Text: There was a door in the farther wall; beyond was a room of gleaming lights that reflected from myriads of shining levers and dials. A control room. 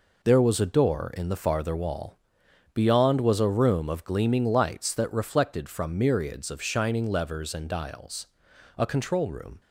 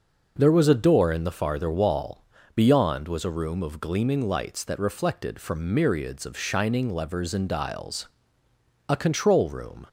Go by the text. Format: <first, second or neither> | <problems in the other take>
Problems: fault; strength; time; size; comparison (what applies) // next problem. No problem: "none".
neither | none